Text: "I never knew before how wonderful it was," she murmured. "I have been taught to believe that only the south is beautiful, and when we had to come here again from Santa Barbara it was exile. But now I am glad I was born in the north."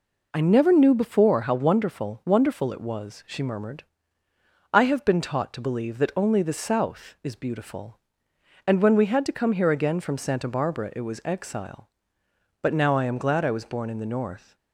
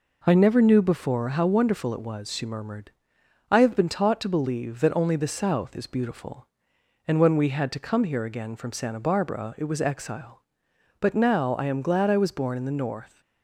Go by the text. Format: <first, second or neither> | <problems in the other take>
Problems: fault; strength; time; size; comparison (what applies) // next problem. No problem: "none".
second | says "wonderful" twice; at 2.2 s